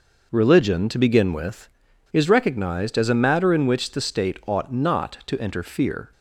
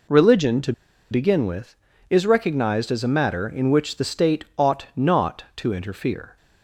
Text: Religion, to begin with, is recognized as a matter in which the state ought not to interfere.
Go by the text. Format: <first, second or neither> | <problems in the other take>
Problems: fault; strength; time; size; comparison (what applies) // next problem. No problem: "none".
first | pauses between "to" and "begin"; at 0.7 s; 0.39 s long